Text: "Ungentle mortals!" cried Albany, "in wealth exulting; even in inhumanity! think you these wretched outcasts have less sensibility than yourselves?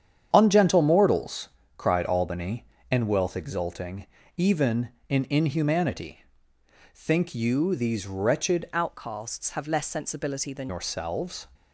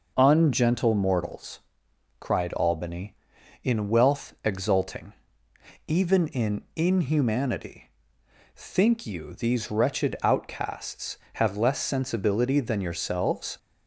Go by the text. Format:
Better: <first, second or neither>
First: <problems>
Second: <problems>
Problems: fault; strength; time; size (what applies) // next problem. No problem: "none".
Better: second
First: starts louder than the rest; strong; until 1.3 s; 8.5 dB // changes voice from "outcasts" to "than"; from 8.7 to 10.6 s; 1.9 s long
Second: none